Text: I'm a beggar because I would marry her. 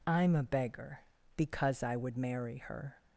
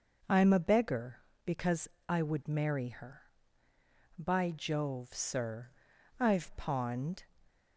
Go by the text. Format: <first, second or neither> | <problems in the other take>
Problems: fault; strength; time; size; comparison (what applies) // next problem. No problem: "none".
first | pauses between "because" and "I"; slight; at 1.8 s; 0.20 s long // goes on to say "By Jove sir I've pawned"; strong; from 4.1 s on; 3.0 s long